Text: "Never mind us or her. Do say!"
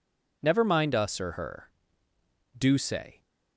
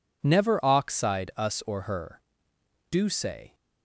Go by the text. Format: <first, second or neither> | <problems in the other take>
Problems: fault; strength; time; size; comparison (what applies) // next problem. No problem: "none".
first | says "oxide" for "mind"; at 0.6 s